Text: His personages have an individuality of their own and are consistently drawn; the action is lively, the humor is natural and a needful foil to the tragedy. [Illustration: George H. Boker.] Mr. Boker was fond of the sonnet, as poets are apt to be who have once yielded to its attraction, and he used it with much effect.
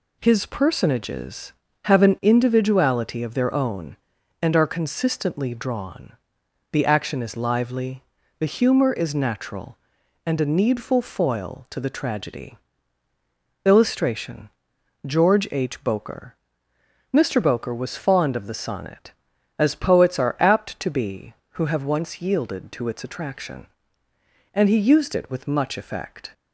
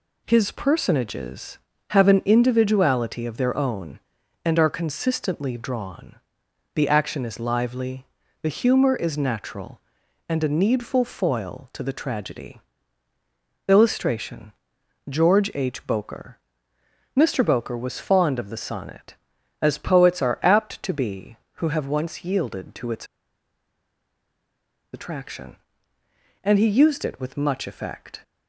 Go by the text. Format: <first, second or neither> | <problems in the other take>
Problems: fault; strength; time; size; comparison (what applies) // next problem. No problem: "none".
first | pauses between "its" and "attraction"; strong; at 23.0 s; 1.8 s long